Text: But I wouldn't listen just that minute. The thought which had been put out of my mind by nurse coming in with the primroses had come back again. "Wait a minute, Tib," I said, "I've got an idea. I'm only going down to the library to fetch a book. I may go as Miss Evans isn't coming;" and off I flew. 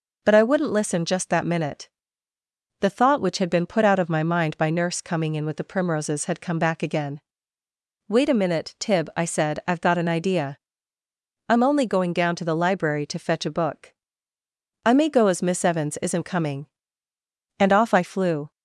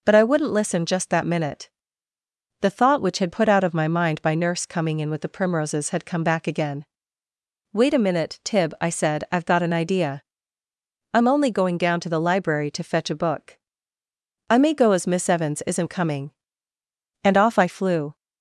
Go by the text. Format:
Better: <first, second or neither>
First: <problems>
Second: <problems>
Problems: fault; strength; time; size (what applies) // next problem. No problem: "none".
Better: first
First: none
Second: skips "been"; at 3.3 s